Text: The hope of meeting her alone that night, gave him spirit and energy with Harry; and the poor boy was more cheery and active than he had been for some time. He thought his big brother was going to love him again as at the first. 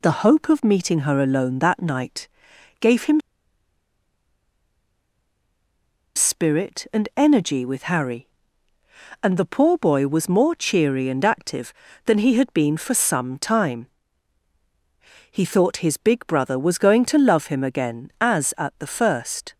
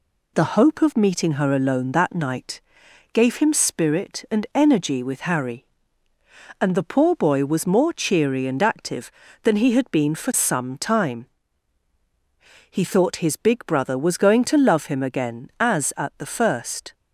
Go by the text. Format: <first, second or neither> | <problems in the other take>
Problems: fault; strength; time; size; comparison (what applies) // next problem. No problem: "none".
second | pauses between "him" and "spirit"; strong; at 3.2 s; 2.9 s long